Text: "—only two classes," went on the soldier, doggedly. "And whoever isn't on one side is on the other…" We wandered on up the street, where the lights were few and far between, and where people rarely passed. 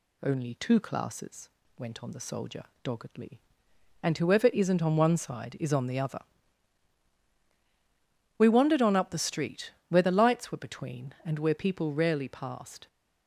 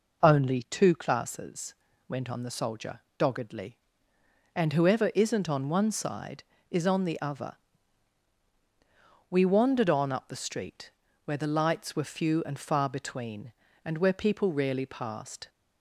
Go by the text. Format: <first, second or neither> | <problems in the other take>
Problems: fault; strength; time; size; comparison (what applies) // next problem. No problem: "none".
second | skips "few and far"; at 10.5 s